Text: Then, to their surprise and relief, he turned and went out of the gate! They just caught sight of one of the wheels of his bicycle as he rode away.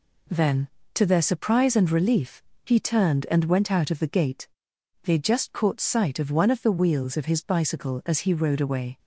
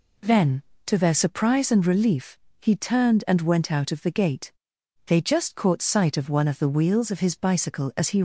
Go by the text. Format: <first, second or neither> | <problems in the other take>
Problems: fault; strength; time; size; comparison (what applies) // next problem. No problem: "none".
first | stops before "rode away"; at 8.1 s